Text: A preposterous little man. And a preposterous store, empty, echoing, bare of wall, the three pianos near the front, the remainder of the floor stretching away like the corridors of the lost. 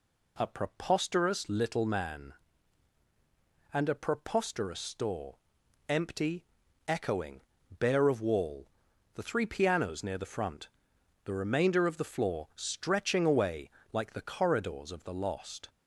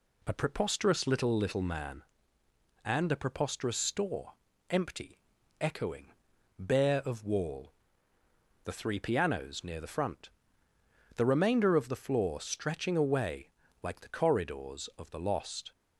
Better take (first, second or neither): first